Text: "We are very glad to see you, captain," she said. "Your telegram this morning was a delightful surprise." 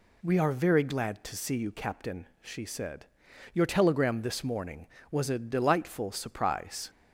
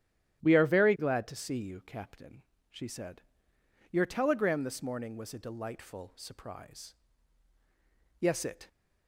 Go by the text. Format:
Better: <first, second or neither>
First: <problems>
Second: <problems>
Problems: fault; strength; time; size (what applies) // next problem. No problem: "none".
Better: first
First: none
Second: starts louder than the rest; strong; until 1.4 s; 10.5 dB // goes on to say "Yes it"; slight; from 8.1 s on; 0.48 s long